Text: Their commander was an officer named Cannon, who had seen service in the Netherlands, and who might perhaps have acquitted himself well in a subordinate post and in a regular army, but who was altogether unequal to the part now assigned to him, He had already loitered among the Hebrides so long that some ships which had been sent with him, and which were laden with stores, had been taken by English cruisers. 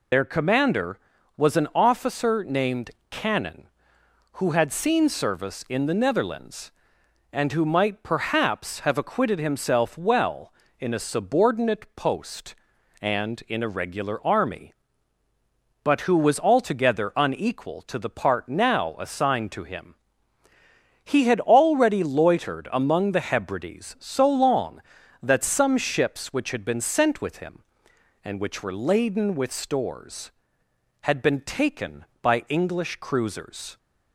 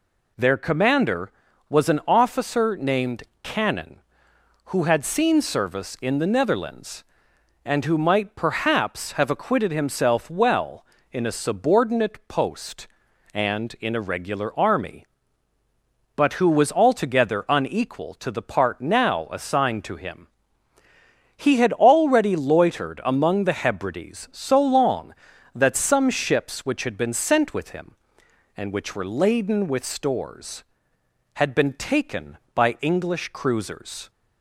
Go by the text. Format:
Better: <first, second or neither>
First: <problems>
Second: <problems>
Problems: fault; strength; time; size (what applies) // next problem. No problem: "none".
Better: second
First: loses the start of "Their"; at 0.1 s; 85 ms // pauses between "named" and "Cannon"; slight; at 2.8 s; 0.20 s long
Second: pauses between "named" and "Cannon"; slight; at 3.2 s; 0.20 s long